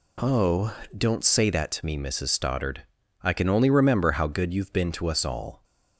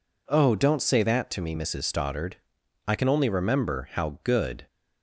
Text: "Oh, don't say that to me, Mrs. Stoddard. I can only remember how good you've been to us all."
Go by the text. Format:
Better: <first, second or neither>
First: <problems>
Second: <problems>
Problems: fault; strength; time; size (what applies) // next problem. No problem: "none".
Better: first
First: none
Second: stops before "you've been to us all"; at 4.6 s